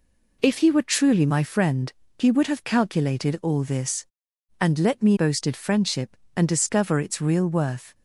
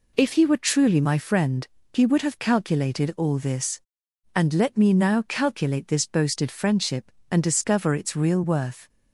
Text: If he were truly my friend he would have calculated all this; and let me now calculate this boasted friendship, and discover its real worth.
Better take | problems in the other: second | pauses between "friend" and "he"; slight; at 1.9 s; 0.24 s long; slight in the second // skips "now calculate this"; at 5.1 s

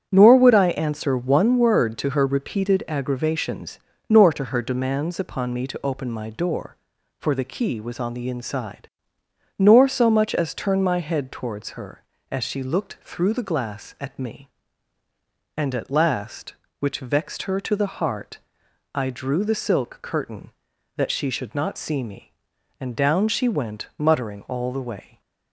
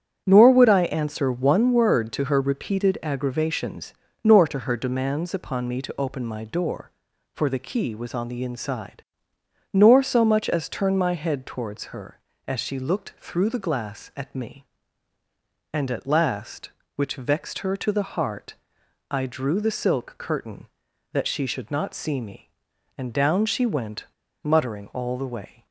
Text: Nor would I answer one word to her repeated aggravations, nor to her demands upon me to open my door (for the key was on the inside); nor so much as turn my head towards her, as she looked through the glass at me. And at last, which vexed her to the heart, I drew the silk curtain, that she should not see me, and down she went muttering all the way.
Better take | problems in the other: first | starts louder than the rest; strong; until 1.2 s; 9 dB; strong in the first // pauses between "went" and "muttering"; at 24.0 s; 0.39 s long

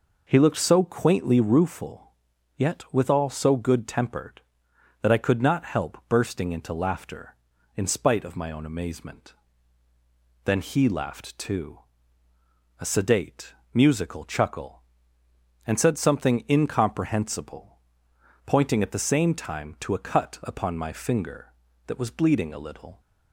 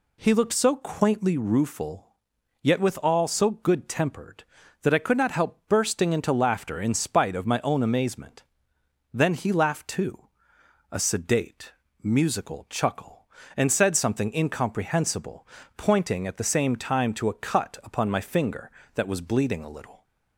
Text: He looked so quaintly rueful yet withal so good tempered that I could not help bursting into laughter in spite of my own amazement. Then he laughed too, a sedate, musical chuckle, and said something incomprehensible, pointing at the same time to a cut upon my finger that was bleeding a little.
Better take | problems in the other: neither | pauses between "rueful" and "yet"; noticeable; the same in both

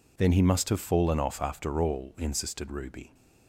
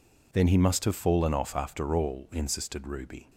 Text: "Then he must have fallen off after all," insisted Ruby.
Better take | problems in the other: neither | none

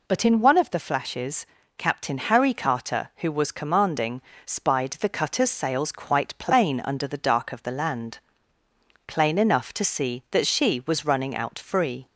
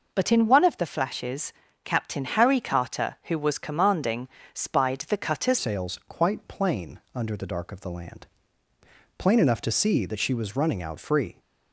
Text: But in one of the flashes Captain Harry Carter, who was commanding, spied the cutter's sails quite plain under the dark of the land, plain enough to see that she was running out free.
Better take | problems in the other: first | pauses between "flashes" and "Captain"; slight; at 1.5 s; 0.32 s long; slight in the first // changes voice at "sails"; from 5.5 s on; 5.8 s long // pauses between "plain" and "under"; slight; at 6.9 s; 0.16 s long

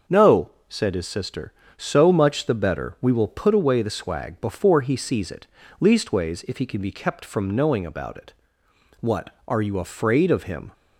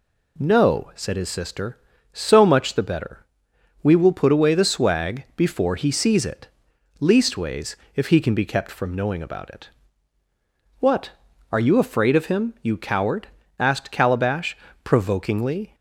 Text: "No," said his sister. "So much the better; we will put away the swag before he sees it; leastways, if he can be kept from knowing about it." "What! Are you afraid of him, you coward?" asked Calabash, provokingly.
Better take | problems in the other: second | starts louder than the rest; until 1.2 s; 6.5 dB // stops before "you coward asked Calabash provokingly"; at 10.7 s

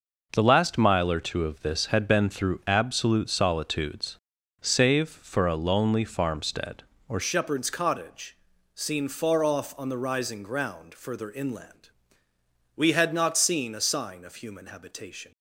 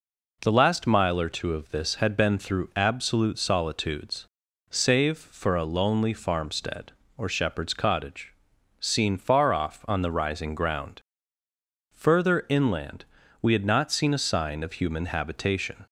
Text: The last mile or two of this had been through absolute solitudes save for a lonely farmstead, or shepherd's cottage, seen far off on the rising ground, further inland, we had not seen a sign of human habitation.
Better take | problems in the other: second | pauses between "solitudes" and "save"; at 4.1 s; 0.42 s long; also in the second // changes voice at "shepherd's"; from 7.2 s on; 8.1 s long

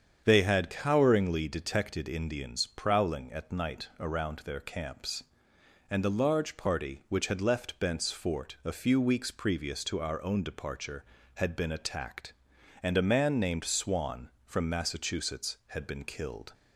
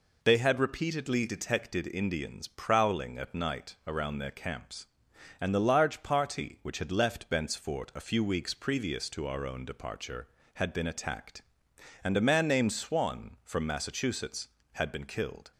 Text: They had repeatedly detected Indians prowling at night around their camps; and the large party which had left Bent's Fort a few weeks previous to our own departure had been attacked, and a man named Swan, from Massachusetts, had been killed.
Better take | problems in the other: second | starts louder than the rest; strong; until 1.2 s; 7.5 dB // says "coweringly" for "repeatedly"; at 0.7 s

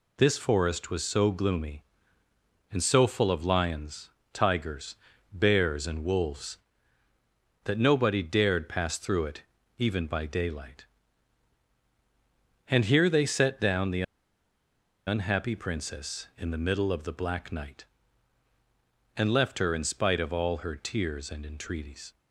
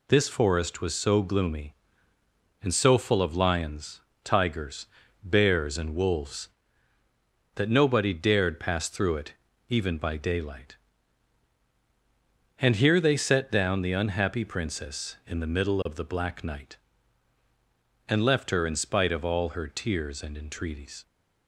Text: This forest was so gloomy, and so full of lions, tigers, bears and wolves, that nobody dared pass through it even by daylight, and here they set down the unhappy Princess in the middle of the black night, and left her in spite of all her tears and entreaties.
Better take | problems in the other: second | pauses between "it" and "even"; slight; at 9.4 s; 0.36 s long; slight in the second // pauses between "the" and "unhappy"; at 14.0 s; 1.0 s long

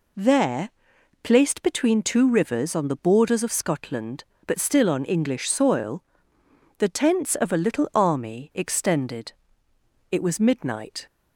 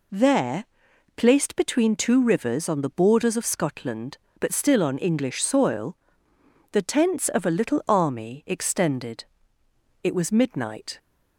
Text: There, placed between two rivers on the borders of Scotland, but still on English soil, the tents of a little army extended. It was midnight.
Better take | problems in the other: neither | none

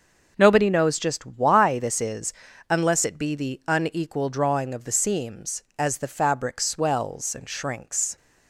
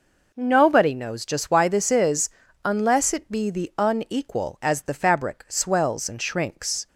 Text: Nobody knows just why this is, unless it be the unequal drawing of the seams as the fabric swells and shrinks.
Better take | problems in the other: first | skips "drawing of the seams"; at 4.5 s

